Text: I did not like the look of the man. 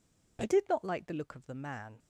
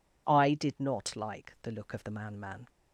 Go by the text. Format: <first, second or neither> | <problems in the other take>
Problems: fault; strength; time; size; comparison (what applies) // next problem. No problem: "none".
first | says "man" twice; at 2.3 s